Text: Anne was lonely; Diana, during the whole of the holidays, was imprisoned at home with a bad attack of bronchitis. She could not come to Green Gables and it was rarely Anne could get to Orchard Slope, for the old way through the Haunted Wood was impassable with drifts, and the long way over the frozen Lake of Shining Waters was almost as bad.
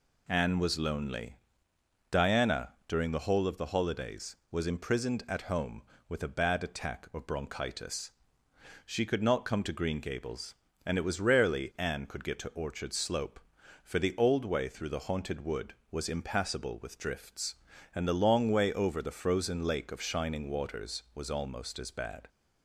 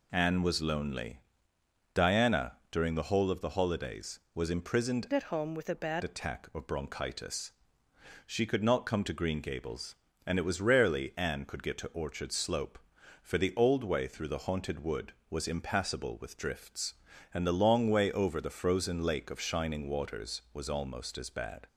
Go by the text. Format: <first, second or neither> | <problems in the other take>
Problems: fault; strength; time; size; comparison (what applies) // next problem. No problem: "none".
first | changes voice from "at" to "bad"; from 5.1 to 6.0 s; 0.9 s long